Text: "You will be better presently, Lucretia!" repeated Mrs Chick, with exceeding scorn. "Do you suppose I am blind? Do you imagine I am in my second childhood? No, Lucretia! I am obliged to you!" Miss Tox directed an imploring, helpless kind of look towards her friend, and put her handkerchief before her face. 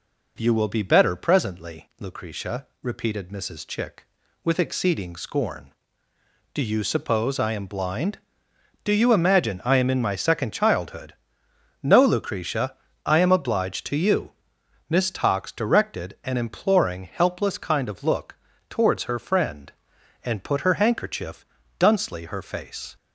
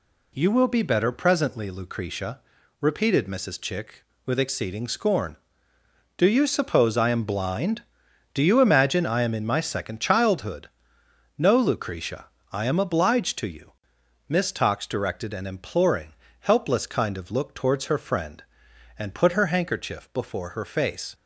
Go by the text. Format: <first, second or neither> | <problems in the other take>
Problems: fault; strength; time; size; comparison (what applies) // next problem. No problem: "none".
second | pauses between "look" and "towards"; slight; at 18.3 s; 0.34 s long // says "duncely" for "before"; at 21.7 s